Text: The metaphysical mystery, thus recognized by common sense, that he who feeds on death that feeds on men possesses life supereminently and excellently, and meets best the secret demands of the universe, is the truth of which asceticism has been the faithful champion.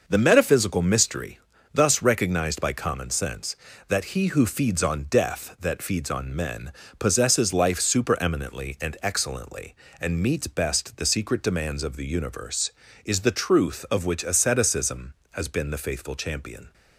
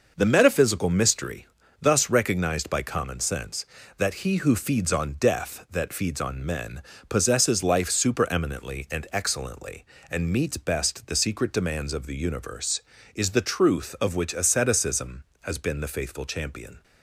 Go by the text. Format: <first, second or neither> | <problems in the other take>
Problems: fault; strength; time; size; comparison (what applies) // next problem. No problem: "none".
neither | pauses between "men" and "possesses"; slight; the same in both